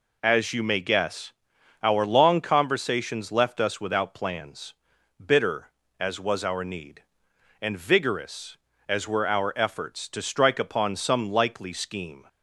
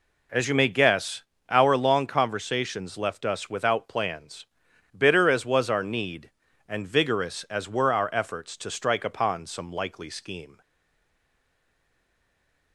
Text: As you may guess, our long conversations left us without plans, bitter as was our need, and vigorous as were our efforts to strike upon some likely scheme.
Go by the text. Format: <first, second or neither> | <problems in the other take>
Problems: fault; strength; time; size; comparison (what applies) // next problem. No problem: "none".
first | stays silent after the last word; from 10.6 s on; 2.1 s long